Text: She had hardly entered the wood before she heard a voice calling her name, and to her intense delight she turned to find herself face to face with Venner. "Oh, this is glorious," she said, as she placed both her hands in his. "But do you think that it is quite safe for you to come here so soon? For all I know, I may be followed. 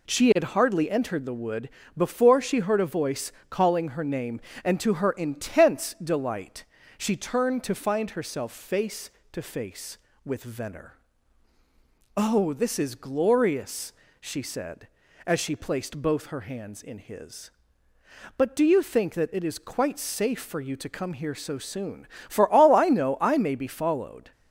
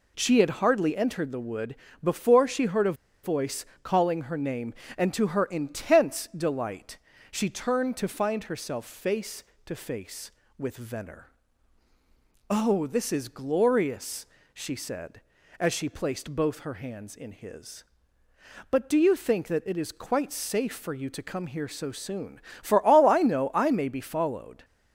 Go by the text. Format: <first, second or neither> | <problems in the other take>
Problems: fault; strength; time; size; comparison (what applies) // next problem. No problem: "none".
first | pauses between "wood" and "before"; slight; at 1.7 s; 0.28 s long; slight in the first // pauses between "a" and "voice"; slight; at 2.9 s; 0.30 s long // pauses between "voice" and "calling"; slight; at 3.6 s; 0.18 s long; slight in the first // pauses between "delight" and "she"; slight; at 6.9 s; 0.32 s long; slight in the first